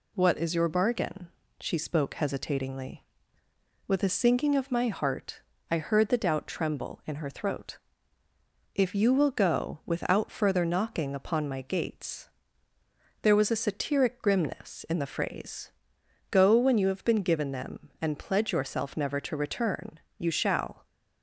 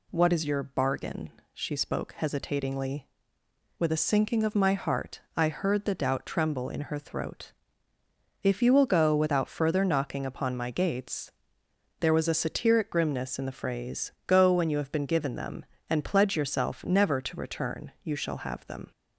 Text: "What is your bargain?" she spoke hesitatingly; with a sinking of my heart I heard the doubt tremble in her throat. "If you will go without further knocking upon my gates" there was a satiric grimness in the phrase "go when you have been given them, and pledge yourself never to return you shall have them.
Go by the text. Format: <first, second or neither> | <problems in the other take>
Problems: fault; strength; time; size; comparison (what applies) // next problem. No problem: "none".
second | pauses between "heart" and "I"; slight; at 5.4 s; 0.32 s long; slight in the second // pauses between "gates" and "there"; noticeable; at 12.2 s; 0.94 s long; noticeable in the second // pauses between "phrase" and "go"; noticeable; at 15.7 s; 0.58 s long // pauses between "return" and "you"; slight; at 19.9 s; 0.20 s long // stops before "have them"; at 20.8 s